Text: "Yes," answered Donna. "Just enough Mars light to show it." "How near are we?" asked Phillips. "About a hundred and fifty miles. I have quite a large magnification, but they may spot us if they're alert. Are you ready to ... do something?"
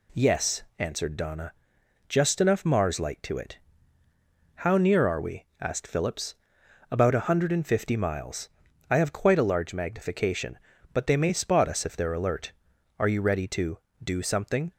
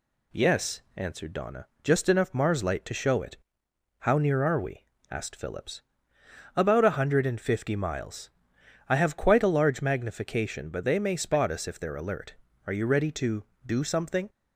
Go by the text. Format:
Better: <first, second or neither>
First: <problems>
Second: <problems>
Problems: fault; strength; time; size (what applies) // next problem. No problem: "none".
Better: second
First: skips "show"; at 3.3 s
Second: none